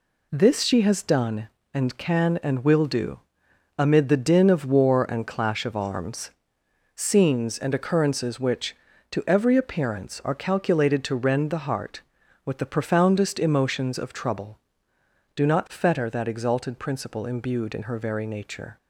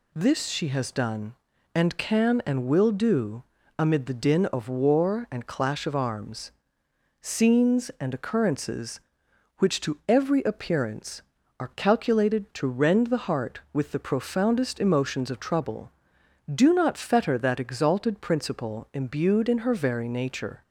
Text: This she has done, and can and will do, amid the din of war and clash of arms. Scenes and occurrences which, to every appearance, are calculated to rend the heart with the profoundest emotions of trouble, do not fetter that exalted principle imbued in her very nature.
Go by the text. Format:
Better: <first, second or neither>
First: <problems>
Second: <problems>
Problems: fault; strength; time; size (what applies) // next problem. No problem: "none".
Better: neither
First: none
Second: none